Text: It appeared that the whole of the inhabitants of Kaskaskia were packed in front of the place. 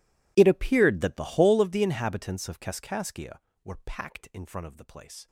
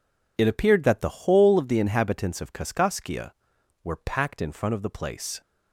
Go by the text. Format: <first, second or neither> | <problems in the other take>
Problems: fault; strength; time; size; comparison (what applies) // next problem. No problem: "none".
second | gets quieter; strong; throughout; 23 dB